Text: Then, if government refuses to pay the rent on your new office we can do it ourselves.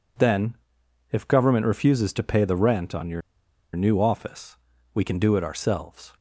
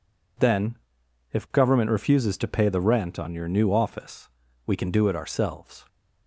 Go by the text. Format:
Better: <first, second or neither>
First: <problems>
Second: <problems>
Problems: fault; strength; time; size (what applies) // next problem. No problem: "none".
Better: second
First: pauses between "your" and "new"; noticeable; at 3.2 s; 0.54 s long // pauses between "office" and "we"; slight; at 4.5 s; 0.36 s long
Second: pauses between "office" and "we"; slight; at 4.2 s; 0.36 s long